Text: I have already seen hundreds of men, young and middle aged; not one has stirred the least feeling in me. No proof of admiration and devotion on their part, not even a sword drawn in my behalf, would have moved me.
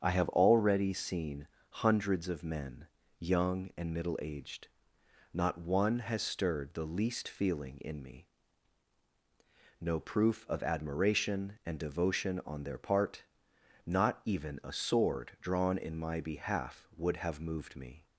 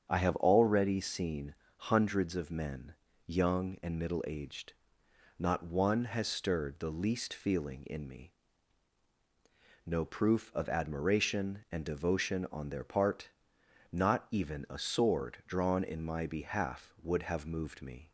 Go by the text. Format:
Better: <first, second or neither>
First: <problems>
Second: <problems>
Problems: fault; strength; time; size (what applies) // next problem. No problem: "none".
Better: neither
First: starts louder than the rest; strong; until 1.0 s; 8 dB // pauses between "seen" and "hundreds"; slight; at 1.4 s; 0.22 s long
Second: starts louder than the rest; strong; until 1.1 s; 8 dB // pauses between "seen" and "hundreds"; slight; at 1.5 s; 0.22 s long